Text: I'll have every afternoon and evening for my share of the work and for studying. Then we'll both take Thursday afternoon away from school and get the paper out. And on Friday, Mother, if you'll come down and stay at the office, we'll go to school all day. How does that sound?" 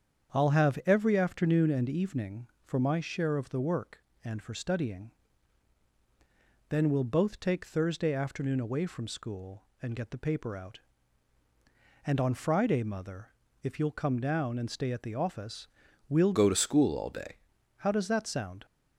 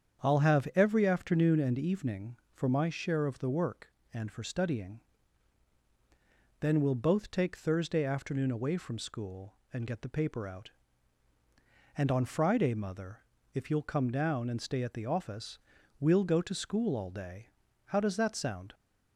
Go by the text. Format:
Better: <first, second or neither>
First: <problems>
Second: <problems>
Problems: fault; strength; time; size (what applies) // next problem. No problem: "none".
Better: second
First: starts louder than the rest; strong; until 1.4 s; 8 dB // changes voice from "go" to "day"; from 16.3 to 17.3 s; 1.0 s long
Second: starts louder than the rest; strong; until 1.3 s; 8 dB